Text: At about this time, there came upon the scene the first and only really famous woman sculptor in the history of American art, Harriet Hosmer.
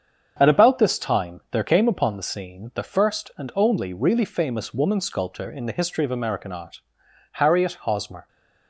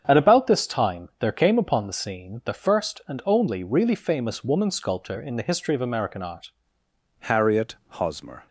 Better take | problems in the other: first | starts louder than the rest; strong; until 1.0 s; 7.5 dB; strong in the first // changes voice at "Harriet"; from 7.2 s on; 1.2 s long // pauses between "Harriet" and "Hosmer"; slight; at 7.7 s; 0.24 s long

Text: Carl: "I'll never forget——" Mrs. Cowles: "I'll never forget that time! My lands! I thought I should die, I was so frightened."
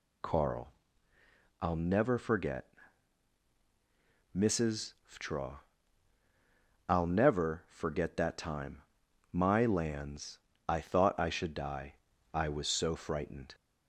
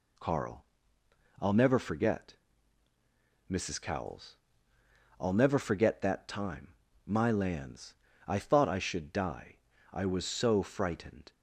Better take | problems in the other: second | says "Ftraw" for "Cowles"; at 5.0 s

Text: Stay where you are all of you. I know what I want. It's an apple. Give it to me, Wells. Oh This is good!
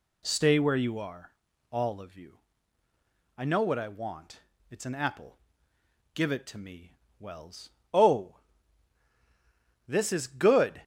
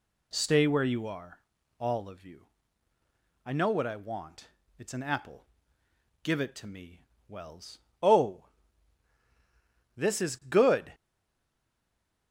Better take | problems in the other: first | pauses between "are" and "all"; at 1.3 s; 0.38 s long; also in the first // pauses between "Oh" and "This"; strong; at 8.4 s; 1.5 s long; strong in the first // stays silent after the last word; noticeable; from 10.9 s on; 1.4 s long

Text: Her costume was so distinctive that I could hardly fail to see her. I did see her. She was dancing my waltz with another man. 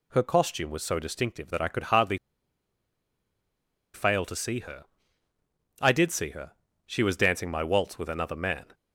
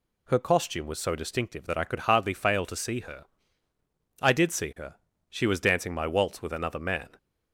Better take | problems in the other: second | pauses between "hardly" and "fail"; strong; at 2.1 s; 1.7 s long

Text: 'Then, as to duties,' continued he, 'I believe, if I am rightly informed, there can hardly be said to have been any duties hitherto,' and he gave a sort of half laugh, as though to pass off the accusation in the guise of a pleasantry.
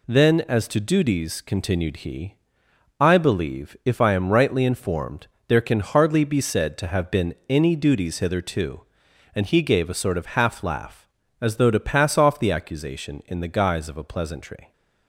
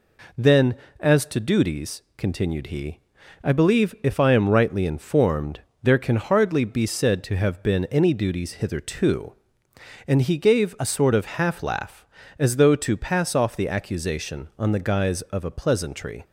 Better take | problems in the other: first | says "on" for "in"; at 14.5 s

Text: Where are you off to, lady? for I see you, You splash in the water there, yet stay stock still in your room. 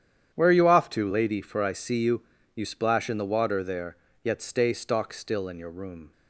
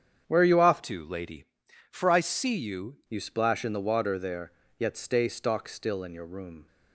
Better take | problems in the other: first | starts louder than the rest; strong; until 1.2 s; 8 dB; strong in the first // changes voice from "to" to "you"; from 0.8 to 2.9 s; 2.1 s long

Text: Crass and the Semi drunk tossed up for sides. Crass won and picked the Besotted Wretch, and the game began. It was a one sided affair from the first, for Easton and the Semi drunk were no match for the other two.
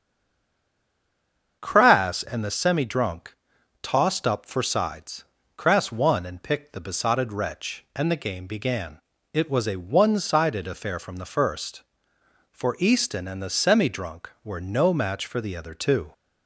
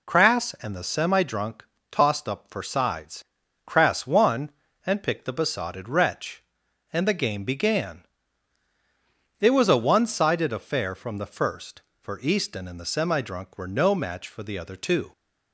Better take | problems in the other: second | stays silent before the first word; noticeable; until 1.6 s; 1.6 s long // starts louder than the rest; until 2.6 s; 6.5 dB // pauses between "drunk" and "tossed"; noticeable; at 3.3 s; 0.48 s long; slight in the second

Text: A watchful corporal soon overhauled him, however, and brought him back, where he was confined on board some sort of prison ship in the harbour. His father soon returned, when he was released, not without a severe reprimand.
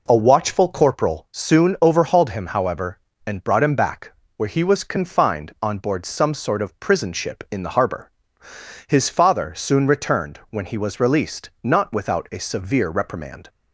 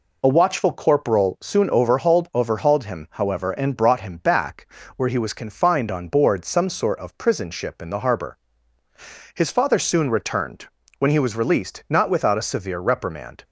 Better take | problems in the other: first | says "overhauled" twice; at 2.3 s

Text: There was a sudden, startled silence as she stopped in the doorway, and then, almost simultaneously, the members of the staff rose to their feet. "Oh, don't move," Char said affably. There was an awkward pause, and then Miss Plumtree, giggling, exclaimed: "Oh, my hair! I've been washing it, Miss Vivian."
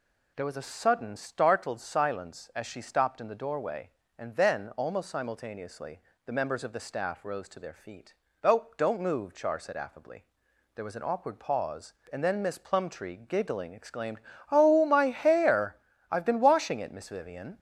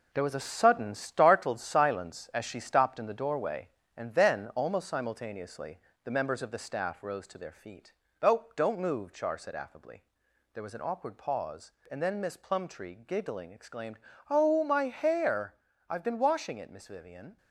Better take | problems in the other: first | gets quieter; noticeable; throughout; 5.5 dB

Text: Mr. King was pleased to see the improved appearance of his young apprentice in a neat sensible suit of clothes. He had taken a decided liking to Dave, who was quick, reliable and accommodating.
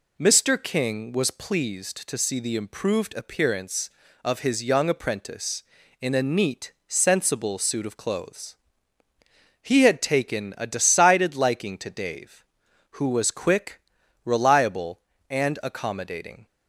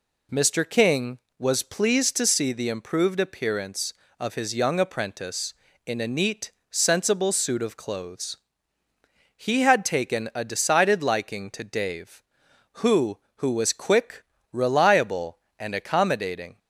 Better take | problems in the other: first | pauses between "neat" and "sensible"; slight; at 6.5 s; 0.18 s long // says "who" twice; at 13.3 s

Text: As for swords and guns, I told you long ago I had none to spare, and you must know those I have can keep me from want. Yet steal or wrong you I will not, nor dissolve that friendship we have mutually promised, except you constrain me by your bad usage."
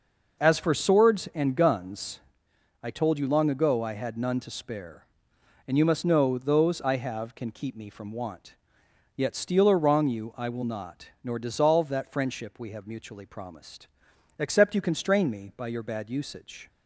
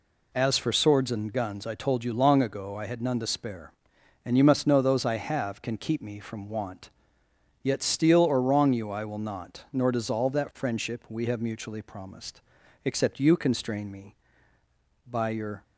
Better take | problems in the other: first | stops before "bad usage"; at 15.6 s

